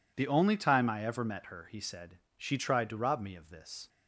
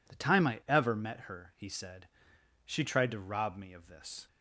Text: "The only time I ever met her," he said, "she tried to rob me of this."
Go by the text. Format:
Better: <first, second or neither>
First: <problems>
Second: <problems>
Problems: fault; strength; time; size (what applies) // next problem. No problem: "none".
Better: first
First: none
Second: skips "only"; at 0.1 s